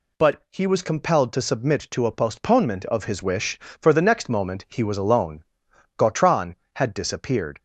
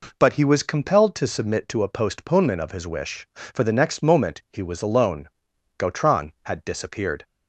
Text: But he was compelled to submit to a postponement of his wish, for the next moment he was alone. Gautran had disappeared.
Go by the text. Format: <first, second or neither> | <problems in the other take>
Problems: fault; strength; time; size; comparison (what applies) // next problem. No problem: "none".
neither | none